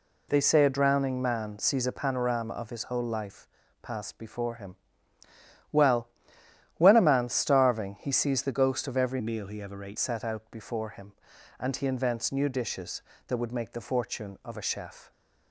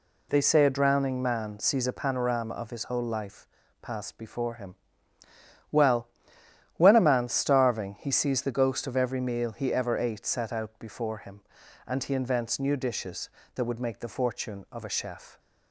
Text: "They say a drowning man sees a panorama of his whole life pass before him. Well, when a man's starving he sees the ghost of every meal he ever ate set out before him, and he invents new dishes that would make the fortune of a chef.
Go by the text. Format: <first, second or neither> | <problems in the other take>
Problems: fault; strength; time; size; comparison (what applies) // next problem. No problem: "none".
second | pauses between "life" and "pass"; slight; at 3.4 s; 0.34 s long; slight in the second // changes voice from "meal" to "ate"; from 9.1 to 9.9 s; 0.8 s long